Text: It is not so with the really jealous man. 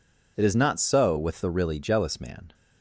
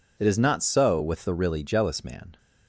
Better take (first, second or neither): neither